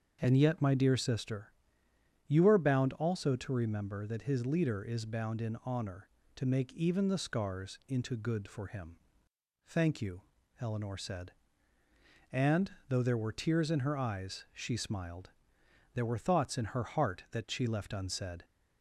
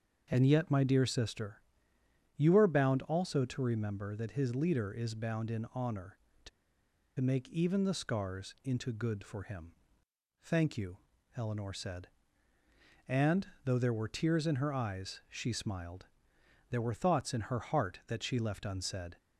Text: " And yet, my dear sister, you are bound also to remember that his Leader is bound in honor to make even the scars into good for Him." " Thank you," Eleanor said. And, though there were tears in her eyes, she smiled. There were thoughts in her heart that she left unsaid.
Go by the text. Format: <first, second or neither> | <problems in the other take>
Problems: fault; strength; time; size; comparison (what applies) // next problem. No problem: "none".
first | starts louder than the rest; until 1.2 s; 7 dB; also in the first // pauses between "to" and "make"; noticeable; at 6.4 s; 0.69 s long